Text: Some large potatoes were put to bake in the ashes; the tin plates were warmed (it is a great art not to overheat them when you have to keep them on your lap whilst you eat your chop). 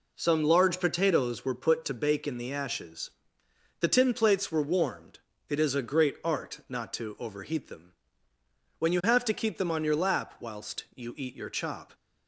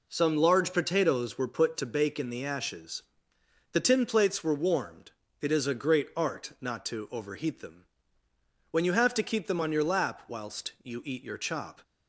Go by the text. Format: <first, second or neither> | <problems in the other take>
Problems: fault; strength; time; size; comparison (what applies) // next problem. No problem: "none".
neither | pauses between "them" and "when"; noticeable; the same in both